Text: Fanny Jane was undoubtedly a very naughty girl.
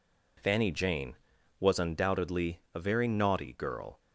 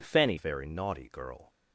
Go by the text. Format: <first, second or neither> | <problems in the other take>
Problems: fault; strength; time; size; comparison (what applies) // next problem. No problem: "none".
first | skips "Jane was undoubtedly a"; at 0.3 s